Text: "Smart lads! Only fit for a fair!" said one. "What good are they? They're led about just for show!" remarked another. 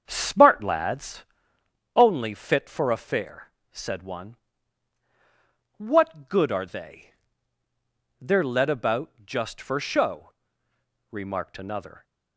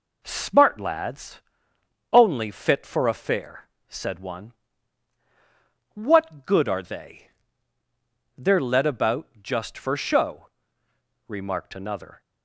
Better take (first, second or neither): second